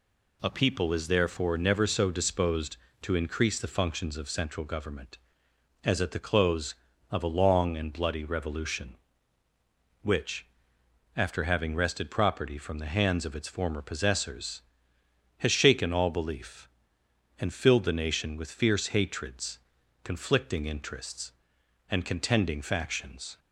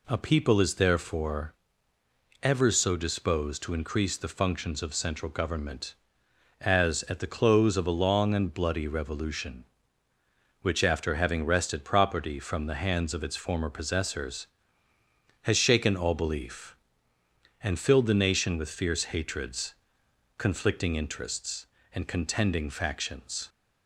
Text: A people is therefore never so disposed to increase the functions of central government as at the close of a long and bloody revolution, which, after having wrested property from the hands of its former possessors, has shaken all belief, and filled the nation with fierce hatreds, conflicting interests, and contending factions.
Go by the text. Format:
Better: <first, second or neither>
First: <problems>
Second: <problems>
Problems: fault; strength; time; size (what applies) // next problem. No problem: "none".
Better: first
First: none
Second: says "ever" for "never"; at 2.4 s